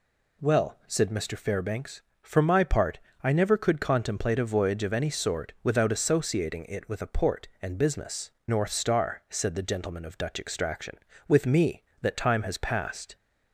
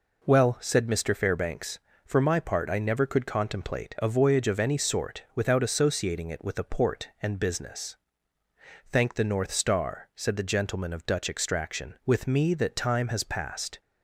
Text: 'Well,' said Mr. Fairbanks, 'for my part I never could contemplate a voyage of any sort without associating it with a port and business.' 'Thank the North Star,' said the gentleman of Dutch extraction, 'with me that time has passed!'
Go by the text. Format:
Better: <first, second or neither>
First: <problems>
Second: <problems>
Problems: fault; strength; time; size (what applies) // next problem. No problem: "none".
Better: second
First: pauses between "part" and "I"; slight; at 2.9 s; 0.24 s long // skips "Thank the"; at 8.3 s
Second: none